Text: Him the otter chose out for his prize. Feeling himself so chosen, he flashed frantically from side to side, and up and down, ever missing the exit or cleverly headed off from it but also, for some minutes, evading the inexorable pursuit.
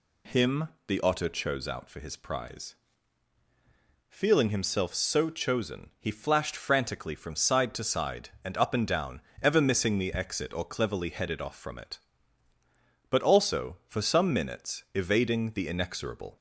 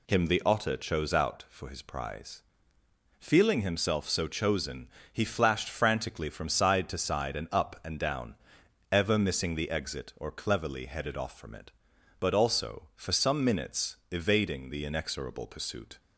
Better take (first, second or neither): second